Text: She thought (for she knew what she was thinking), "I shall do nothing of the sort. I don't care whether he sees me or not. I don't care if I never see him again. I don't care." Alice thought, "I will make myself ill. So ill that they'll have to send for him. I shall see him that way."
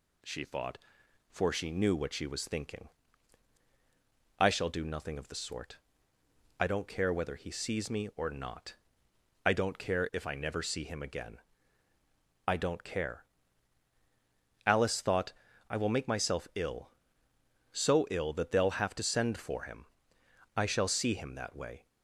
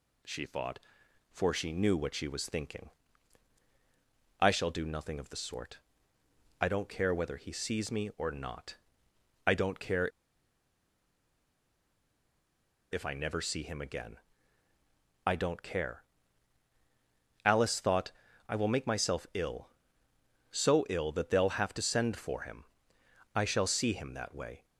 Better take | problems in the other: first | pauses between "care" and "if"; strong; at 10.0 s; 2.8 s long

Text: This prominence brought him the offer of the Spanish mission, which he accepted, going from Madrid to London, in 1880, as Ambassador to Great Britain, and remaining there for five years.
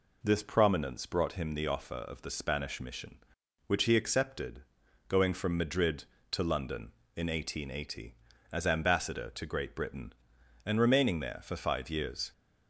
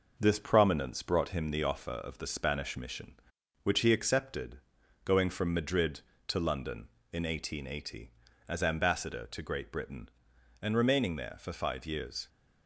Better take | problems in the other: first | gets quieter; throughout; 3.5 dB

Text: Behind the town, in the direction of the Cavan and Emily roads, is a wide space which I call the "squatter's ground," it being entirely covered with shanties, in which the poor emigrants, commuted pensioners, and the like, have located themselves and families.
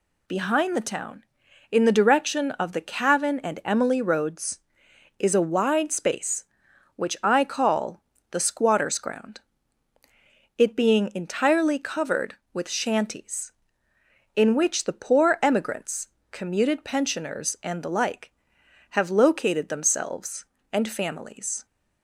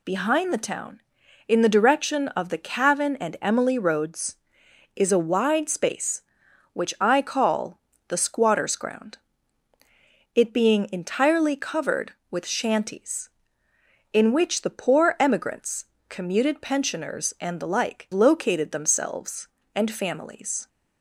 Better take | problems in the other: first | pauses between "call" and "the"; slight; at 7.7 s; 0.30 s long; slight in the first // skips "have"; at 18.1 s

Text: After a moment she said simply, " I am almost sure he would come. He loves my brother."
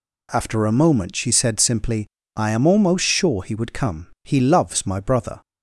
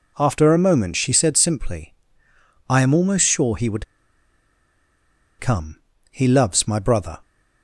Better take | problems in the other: first | pauses between "would" and "come"; strong; at 3.8 s; 1.5 s long

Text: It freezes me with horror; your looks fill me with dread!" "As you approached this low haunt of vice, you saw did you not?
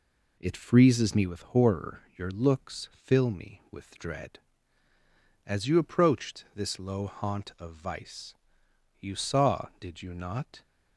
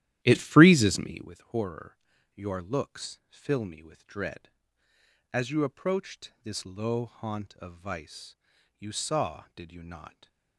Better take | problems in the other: first | starts louder than the rest; strong; until 1.3 s; 13 dB // stays silent after the last word; slight; from 10.0 s on; 0.5 s long

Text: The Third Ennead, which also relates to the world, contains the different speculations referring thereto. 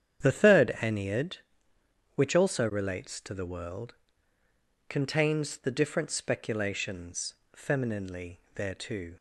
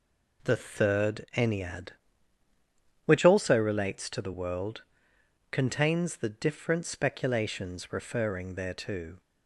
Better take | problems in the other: second | starts louder than the rest; strong; until 1.2 s; 9 dB // says "femininely" for "referring"; at 7.5 s

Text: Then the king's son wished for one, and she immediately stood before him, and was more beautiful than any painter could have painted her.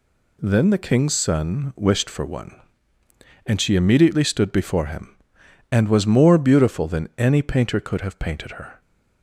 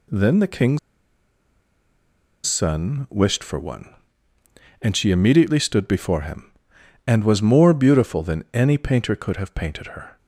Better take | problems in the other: first | pauses between "king's" and "son"; strong; at 0.7 s; 1.6 s long

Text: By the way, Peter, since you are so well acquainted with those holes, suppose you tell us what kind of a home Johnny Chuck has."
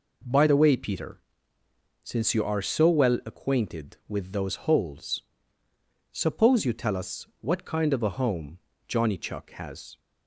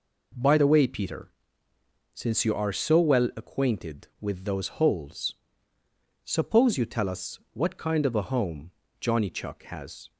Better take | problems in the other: neither | pauses between "home" and "Johnny"; slight; the same in both

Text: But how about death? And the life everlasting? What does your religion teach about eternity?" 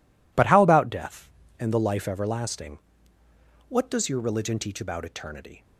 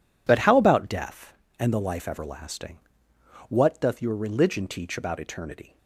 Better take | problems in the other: first | says "doth" for "does"; at 3.7 s

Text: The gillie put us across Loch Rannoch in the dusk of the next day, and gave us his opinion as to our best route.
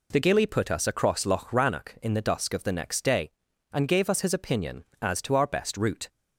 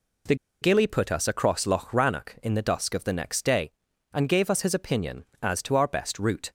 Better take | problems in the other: first | pauses between "The" and "gillie"; slight; at 0.3 s; 0.27 s long

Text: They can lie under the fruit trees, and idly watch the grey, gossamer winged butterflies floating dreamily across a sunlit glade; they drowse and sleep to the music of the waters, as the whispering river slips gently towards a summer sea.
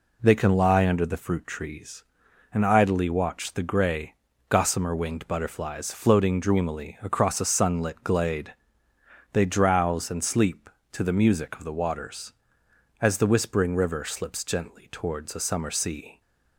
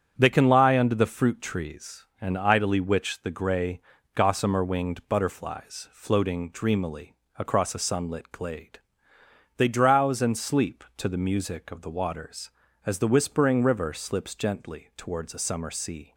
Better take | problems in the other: first | starts louder than the rest; strong; until 1.1 s; 8 dB // says "witch" for "watch"; at 2.7 s // pauses between "dreamily" and "across"; slight; at 7.1 s; 0.22 s long

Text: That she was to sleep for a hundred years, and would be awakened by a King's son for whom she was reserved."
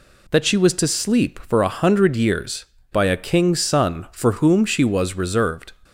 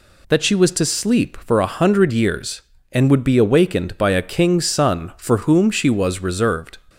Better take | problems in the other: second | skips "and would be awakened"; at 2.7 s

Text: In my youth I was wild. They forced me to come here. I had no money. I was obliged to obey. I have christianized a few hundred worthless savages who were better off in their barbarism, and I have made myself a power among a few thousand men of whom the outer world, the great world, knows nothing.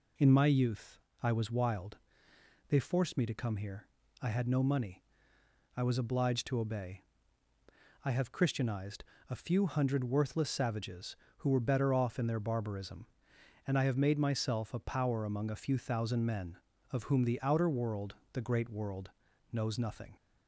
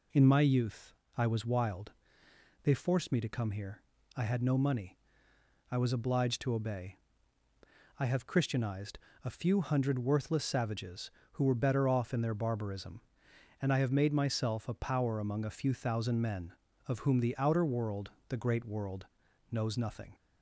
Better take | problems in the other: neither | pauses between "youth" and "I"; slight; the same in both // pauses between "christianized" and "a"; slight; the same in both

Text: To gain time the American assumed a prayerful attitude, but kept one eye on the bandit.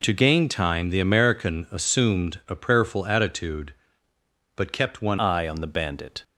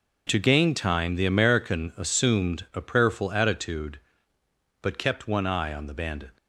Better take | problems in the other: second | changes voice at "eye"; from 5.1 s on; 1.1 s long

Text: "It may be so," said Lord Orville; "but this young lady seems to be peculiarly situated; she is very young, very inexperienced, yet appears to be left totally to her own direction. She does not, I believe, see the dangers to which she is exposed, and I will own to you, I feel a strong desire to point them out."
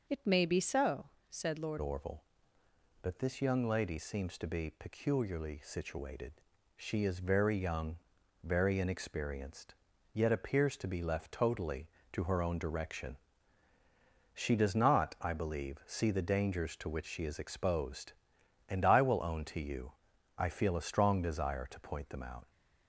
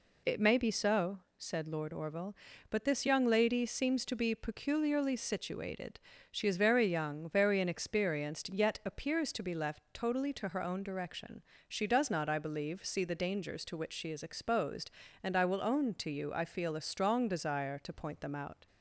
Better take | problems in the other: second | changes voice at "Orville"; from 1.8 s on; 20.6 s long

